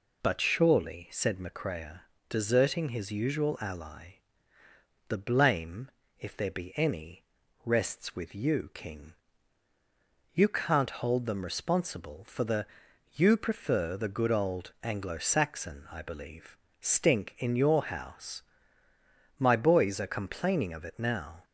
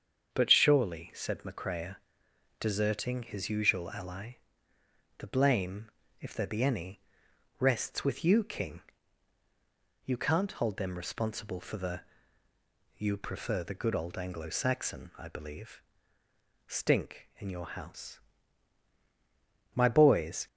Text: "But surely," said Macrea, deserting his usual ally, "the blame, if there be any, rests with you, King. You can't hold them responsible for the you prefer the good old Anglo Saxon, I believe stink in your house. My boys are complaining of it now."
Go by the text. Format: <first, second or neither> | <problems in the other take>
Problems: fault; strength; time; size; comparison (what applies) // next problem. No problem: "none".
first | starts louder than the rest; until 1.3 s; 7 dB // pauses between "the" and "you"; noticeable; at 12.0 s; 0.94 s long; noticeable in the first // pauses between "believe" and "stink"; noticeable; at 15.8 s; 0.86 s long; slight in the first // stops before "are complaining of it now"; at 20.4 s